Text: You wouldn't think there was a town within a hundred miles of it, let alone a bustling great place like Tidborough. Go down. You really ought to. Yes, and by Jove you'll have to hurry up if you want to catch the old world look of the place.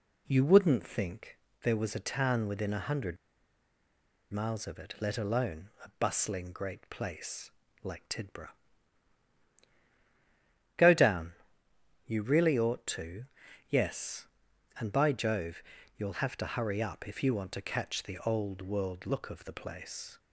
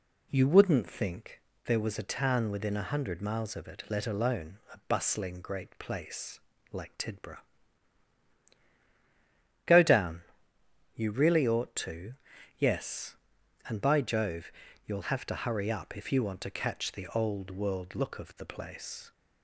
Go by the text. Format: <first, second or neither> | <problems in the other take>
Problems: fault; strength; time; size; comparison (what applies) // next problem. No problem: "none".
second | pauses between "think" and "there"; slight; at 1.3 s; 0.24 s long; slight in the second // pauses between "hundred" and "miles"; at 3.1 s; 1.1 s long // pauses between "place" and "like"; slight; at 7.4 s; 0.32 s long; slight in the second // pauses between "Jove" and "you'll"; slight; at 15.6 s; 0.32 s long; slight in the second